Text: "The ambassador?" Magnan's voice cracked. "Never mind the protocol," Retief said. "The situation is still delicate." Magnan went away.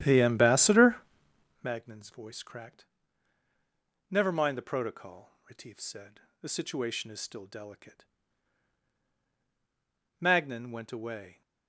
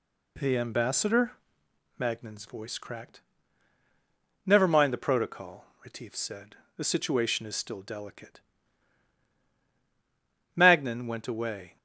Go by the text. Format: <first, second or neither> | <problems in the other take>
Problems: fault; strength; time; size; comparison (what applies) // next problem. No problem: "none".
second | starts louder than the rest; strong; until 1.7 s; 11 dB